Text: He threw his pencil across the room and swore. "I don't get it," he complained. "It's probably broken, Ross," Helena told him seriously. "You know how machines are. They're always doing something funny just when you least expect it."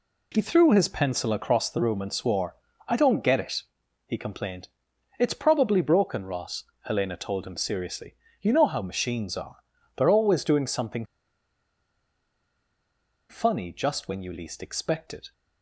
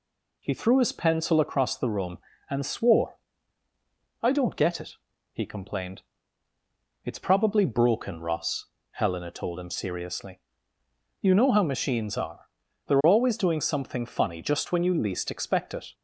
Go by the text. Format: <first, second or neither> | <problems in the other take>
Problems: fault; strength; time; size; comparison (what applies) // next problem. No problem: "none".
second | pauses between "something" and "funny"; strong; at 11.0 s; 2.2 s long